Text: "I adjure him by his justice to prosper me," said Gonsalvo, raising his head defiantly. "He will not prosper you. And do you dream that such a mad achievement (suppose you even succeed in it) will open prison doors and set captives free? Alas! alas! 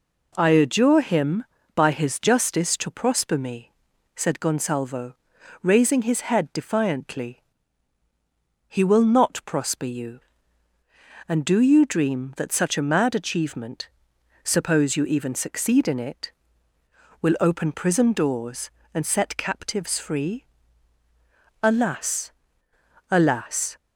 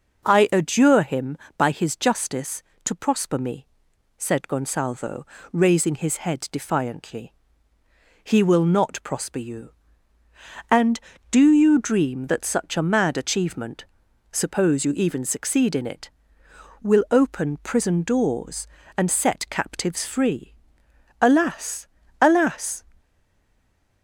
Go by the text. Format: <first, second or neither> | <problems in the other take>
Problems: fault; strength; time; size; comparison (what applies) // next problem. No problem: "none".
first | stays silent after the last word; from 22.9 s on; 1.1 s long